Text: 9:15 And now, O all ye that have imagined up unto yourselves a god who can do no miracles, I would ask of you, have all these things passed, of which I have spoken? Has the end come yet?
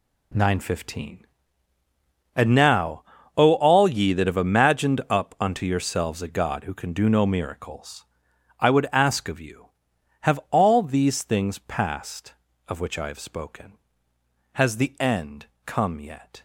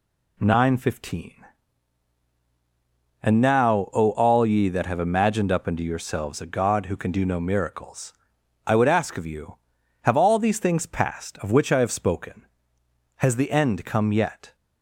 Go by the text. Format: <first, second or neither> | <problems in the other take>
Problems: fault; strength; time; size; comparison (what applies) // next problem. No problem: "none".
second | gets quieter; strong; throughout; 11 dB // pauses between "end" and "come"; slight; at 15.4 s; 0.20 s long